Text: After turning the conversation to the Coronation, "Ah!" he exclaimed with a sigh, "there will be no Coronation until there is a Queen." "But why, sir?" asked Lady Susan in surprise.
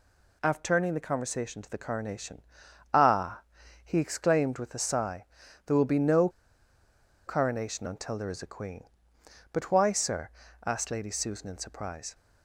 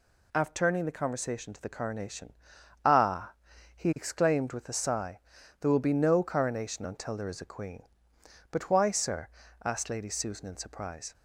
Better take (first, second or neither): second